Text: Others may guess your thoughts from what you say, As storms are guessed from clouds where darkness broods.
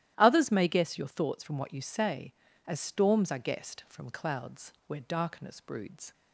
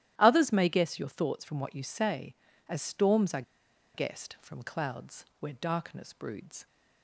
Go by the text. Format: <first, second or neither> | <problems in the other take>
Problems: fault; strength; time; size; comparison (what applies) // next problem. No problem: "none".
first | starts louder than the rest; strong; until 1.1 s; 13 dB; strong in the first // pauses between "are" and "guessed"; noticeable; at 3.4 s; 0.52 s long // pauses between "clouds" and "where"; slight; at 5.2 s; 0.16 s long; slight in the first